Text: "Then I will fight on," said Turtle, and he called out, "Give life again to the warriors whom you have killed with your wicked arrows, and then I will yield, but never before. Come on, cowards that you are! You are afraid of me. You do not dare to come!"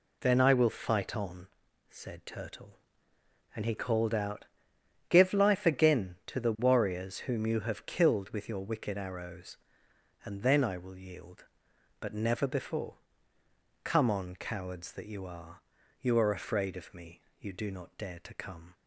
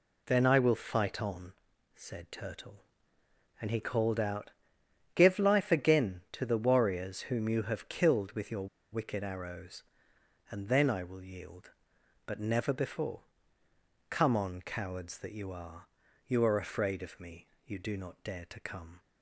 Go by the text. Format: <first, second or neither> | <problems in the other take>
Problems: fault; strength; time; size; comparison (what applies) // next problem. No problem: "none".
first | pauses between "your" and "wicked"; slight; at 8.6 s; 0.24 s long